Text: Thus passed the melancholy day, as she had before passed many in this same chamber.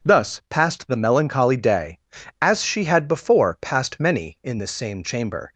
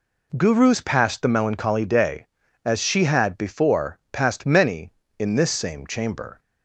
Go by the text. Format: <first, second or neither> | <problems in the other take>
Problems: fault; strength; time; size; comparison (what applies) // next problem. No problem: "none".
first | says "Gurus" for "Thus"; at 0.3 s